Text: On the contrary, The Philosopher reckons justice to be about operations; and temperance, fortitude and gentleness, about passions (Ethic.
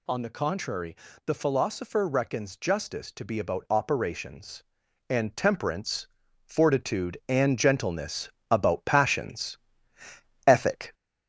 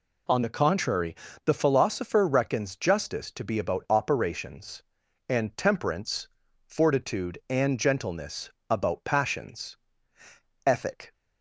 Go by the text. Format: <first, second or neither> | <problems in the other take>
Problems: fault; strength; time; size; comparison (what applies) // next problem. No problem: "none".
second | gets louder; slight; throughout; 3 dB